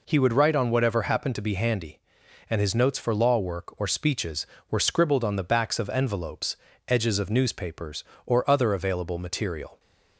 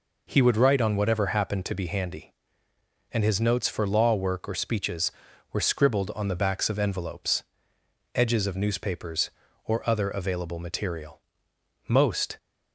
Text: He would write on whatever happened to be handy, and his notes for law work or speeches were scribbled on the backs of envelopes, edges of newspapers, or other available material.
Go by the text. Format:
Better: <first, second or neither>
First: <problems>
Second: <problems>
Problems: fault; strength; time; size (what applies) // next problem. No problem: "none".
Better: first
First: none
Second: goes on to say "Most"; slight; from 11.8 s on; 0.48 s long